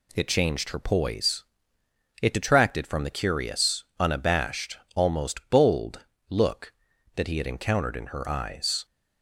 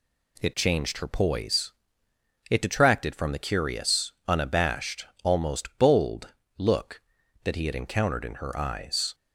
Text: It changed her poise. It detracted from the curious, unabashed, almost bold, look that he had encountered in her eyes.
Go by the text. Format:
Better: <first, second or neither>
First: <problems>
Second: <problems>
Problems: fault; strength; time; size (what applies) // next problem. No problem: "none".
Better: neither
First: none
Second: none